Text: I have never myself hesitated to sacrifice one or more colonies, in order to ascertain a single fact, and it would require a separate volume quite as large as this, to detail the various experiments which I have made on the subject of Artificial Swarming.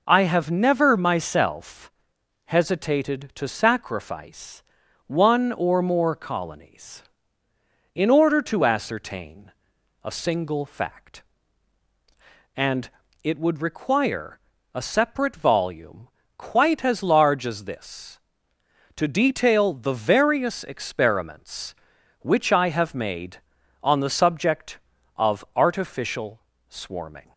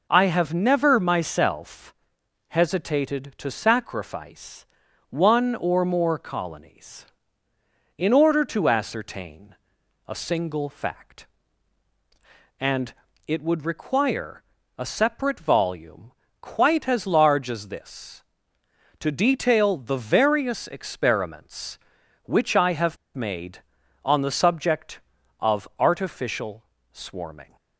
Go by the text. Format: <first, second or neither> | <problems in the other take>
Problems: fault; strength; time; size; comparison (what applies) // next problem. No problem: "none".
first | pauses between "myself" and "hesitated"; noticeable; at 1.9 s; 0.56 s long; noticeable in the first // pauses between "sacrifice" and "one"; noticeable; at 4.6 s; 0.46 s long; noticeable in the first // pauses between "ascertain" and "a"; noticeable; at 9.5 s; 0.50 s long; noticeable in the first // pauses between "and" and "it"; slight; at 12.9 s; 0.34 s long; slight in the first // pauses between "require" and "a"; slight; at 14.4 s; 0.34 s long; slight in the first // pauses between "volume" and "quite"; slight; at 16.1 s; 0.28 s long; slight in the first // pauses between "have" and "made"; slight; at 22.9 s; 0.18 s long // pauses between "Artificial" and "Swarming"; slight; at 26.6 s; 0.28 s long; slight in the first